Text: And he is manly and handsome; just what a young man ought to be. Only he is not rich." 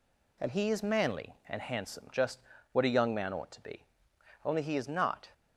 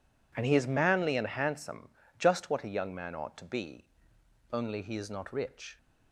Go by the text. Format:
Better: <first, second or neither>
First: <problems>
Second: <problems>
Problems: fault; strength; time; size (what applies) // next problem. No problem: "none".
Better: second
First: pauses between "just" and "what"; slight; at 2.3 s; 0.32 s long // stops before "rich"; at 5.3 s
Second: none